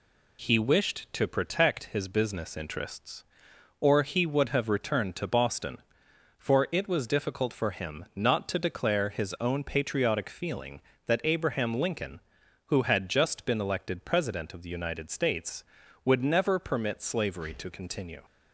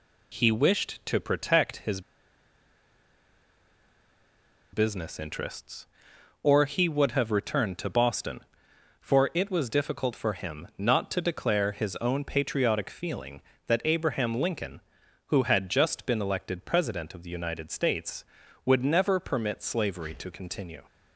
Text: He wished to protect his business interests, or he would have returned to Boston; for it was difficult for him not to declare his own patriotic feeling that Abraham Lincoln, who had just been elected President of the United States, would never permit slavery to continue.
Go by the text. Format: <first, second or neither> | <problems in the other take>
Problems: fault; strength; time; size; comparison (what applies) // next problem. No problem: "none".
first | pauses between "his" and "business"; strong; at 2.0 s; 2.7 s long